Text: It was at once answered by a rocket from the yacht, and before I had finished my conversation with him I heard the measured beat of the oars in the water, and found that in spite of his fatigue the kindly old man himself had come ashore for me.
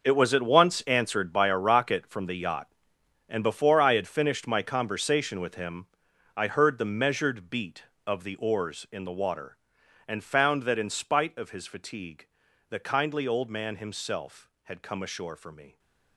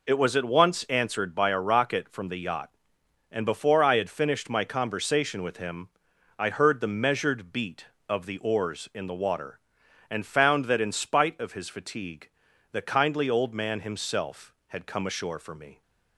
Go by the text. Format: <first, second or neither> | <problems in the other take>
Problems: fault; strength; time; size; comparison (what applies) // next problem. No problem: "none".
second | gets quieter; strong; throughout; 13.5 dB // pauses between "him" and "I"; noticeable; at 5.8 s; 0.48 s long; noticeable in the second // pauses between "fatigue" and "the"; at 12.2 s; 0.44 s long; also in the second